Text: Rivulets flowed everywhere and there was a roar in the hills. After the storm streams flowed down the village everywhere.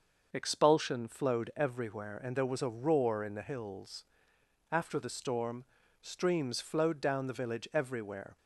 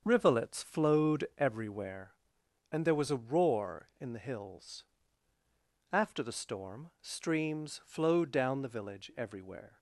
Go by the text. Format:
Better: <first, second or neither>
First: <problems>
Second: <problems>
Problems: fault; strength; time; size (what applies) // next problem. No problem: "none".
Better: second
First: starts louder than the rest; until 1.3 s; 6 dB // says "Expulsion" for "Rivulets"; at 0.3 s // pauses between "storm" and "streams"; slight; at 5.6 s; 0.36 s long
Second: starts louder than the rest; until 1.0 s; 7 dB